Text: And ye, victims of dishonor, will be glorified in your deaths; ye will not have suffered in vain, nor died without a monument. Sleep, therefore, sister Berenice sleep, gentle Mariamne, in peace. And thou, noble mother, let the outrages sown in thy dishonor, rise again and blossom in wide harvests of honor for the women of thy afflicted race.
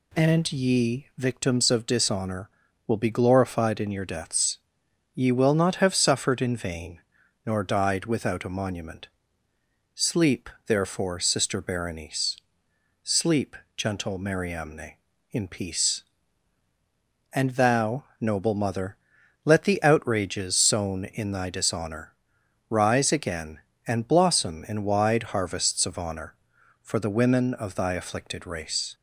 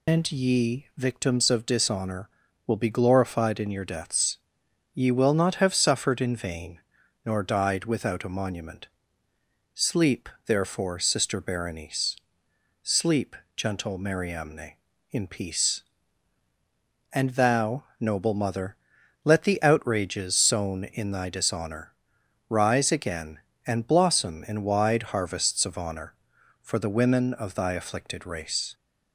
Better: first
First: pauses between "Berenice" and "sleep"; noticeable; at 12.3 s; 0.68 s long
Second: loses the start of "And"; at 0.0 s; 155 ms // pauses between "Berenice" and "sleep"; noticeable; at 12.1 s; 0.68 s long

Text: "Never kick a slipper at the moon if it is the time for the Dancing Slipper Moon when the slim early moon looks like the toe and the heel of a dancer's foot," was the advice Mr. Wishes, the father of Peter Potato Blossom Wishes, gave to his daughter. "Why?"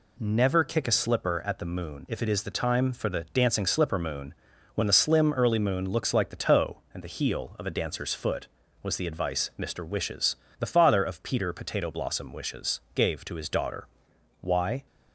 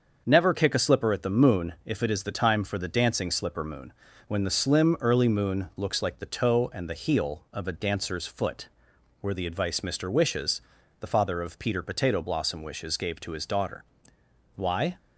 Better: first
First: pauses between "Moon" and "when"; at 4.3 s; 0.40 s long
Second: starts louder than the rest; until 1.2 s; 6.5 dB // pauses between "Moon" and "when"; slight; at 3.9 s; 0.36 s long // says "were" for "was"; at 9.1 s

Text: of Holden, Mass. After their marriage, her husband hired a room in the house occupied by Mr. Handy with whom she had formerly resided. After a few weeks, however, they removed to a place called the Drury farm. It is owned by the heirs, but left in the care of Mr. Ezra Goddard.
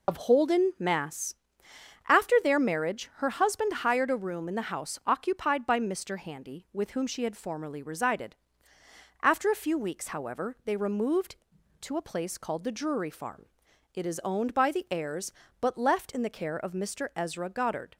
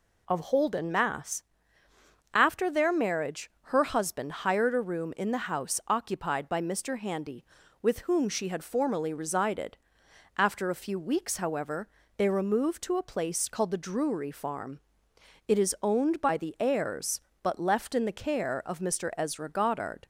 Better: second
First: loses the start of "of"; at 0.0 s; 35 ms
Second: none

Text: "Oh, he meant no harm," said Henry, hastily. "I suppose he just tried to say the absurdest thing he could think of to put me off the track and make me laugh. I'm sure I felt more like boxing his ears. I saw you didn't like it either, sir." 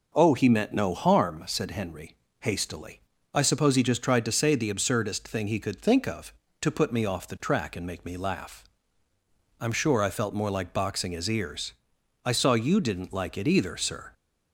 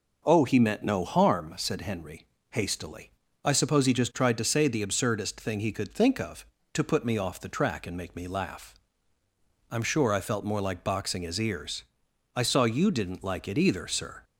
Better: neither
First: none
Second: none

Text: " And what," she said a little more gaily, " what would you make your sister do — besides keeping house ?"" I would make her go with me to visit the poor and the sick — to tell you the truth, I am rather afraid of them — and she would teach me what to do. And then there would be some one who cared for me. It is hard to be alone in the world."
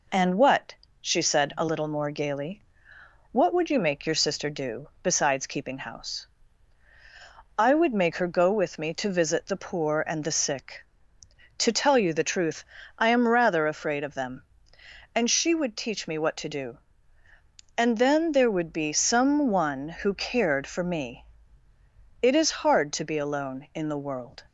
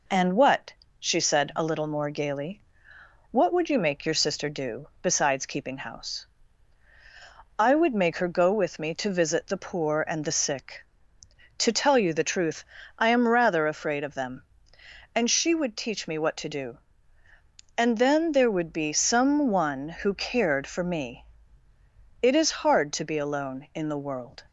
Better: neither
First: none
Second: none

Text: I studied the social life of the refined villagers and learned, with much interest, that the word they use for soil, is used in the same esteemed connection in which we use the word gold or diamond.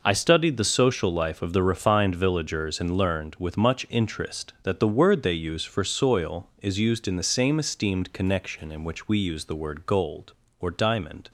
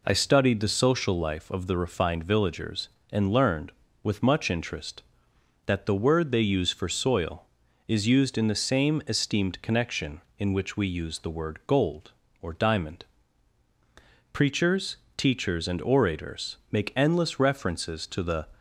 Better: first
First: none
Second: goes on to say "Preachers teachers and orators make endless references to the"; strong; from 14.3 s on; 4.1 s long

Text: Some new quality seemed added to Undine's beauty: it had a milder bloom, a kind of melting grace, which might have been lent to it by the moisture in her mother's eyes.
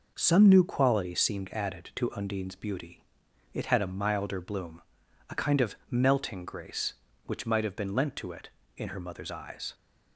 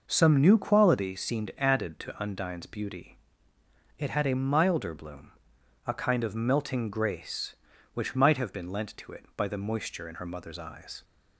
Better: second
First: skips "by the moisture"; at 8.6 s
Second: none

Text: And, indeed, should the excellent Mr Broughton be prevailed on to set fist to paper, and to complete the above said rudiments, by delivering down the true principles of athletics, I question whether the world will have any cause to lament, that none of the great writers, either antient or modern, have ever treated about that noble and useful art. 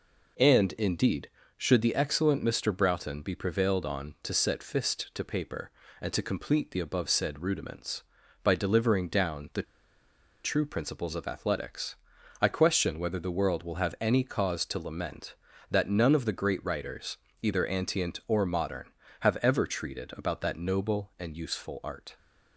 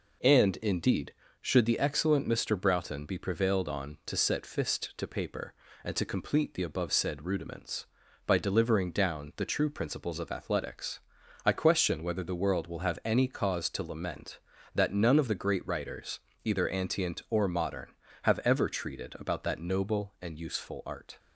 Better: second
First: pauses between "the" and "true"; noticeable; at 9.6 s; 0.81 s long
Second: none

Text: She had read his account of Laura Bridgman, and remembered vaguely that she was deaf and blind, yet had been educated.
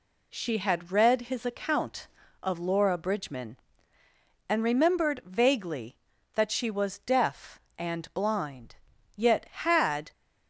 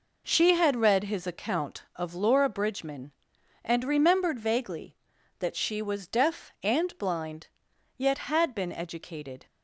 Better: second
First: stops before "been educated"; at 10.1 s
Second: none

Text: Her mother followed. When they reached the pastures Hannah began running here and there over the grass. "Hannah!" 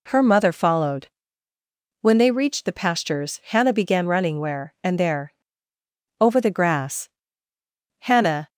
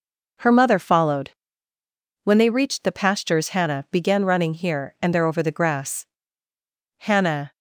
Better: second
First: says "where" for "here"; at 4.3 s // pauses between "there" and "over"; noticeable; at 5.3 s; 0.88 s long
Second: none

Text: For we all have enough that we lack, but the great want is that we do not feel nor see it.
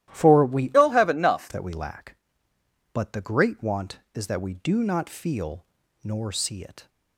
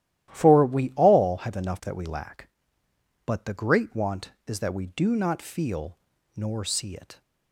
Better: second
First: starts louder than the rest; strong; until 1.1 s; 13 dB // changes voice from "all" to "enough"; from 0.7 to 1.4 s; 0.7 s long // pauses between "feel" and "nor"; at 5.6 s; 0.38 s long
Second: starts louder than the rest; strong; until 1.3 s; 13 dB // pauses between "feel" and "nor"; at 5.9 s; 0.38 s long

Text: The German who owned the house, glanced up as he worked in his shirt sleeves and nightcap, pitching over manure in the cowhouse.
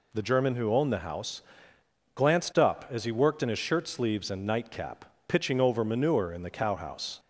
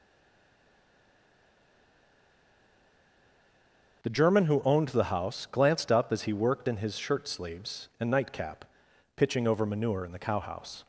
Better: first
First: none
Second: stays silent before the first word; strong; until 4.0 s; 4.0 s long // starts louder than the rest; until 5.0 s; 6.5 dB

